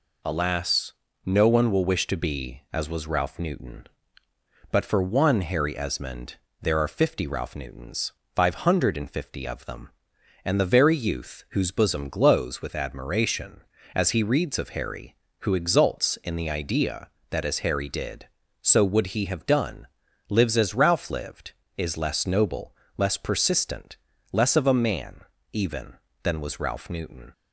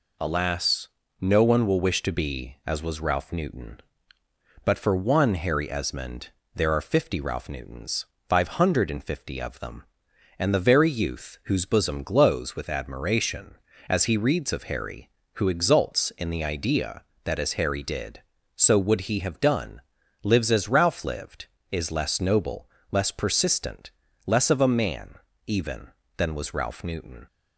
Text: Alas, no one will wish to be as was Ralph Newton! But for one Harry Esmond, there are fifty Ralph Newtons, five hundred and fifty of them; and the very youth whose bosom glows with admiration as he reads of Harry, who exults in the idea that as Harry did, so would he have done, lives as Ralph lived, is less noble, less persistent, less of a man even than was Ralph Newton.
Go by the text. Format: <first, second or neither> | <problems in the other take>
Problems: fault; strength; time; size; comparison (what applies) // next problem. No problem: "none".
neither | pauses between "man" and "even"; slight; the same in both